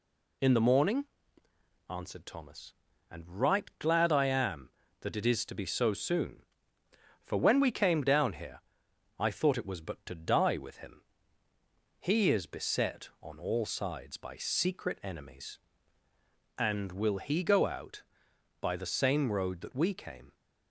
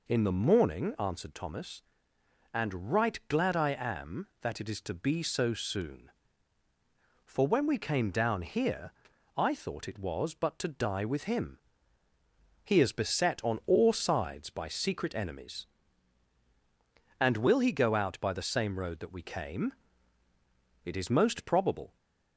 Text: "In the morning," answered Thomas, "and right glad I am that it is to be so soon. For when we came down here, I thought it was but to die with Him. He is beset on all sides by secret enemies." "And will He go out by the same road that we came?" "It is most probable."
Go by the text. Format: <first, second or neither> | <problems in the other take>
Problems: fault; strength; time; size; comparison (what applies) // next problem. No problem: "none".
second | stops before "It is most probable"; at 20.3 s